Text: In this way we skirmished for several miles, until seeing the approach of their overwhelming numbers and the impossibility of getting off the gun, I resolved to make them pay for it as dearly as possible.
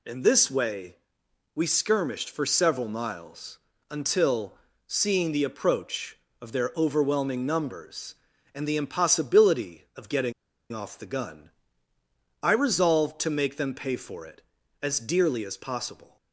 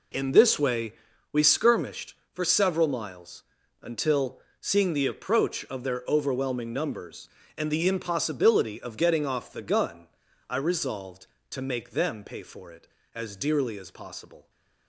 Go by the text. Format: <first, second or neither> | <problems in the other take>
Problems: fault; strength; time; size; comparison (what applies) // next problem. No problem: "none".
second | pauses between "way" and "we"; noticeable; at 0.9 s; 0.60 s long; also in the second // pauses between "until" and "seeing"; slight; at 4.5 s; 0.34 s long; slight in the second // pauses between "getting" and "off"; at 10.3 s; 0.39 s long